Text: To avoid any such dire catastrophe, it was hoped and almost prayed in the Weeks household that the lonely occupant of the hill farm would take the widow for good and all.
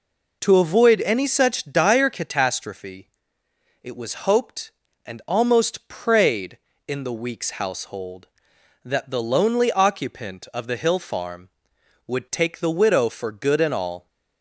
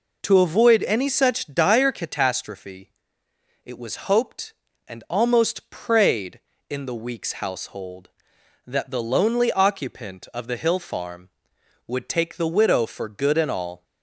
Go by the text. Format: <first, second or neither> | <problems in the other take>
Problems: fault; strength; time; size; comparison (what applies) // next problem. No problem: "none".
neither | none